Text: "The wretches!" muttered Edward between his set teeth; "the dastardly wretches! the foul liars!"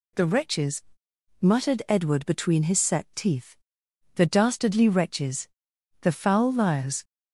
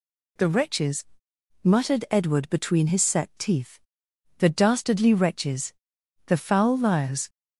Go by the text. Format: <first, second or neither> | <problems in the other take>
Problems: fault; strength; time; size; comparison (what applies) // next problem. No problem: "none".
neither | none